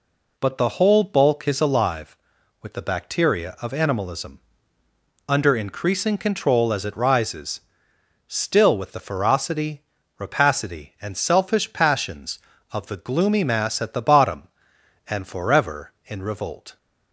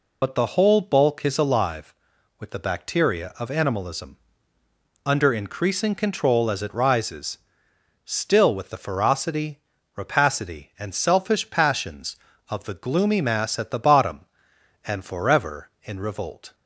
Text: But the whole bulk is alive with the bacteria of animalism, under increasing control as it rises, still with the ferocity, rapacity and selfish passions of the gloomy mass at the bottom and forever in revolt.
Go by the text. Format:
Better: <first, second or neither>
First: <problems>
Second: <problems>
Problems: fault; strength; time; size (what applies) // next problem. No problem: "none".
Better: first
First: none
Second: loses the start of "But"; at 0.2 s; 60 ms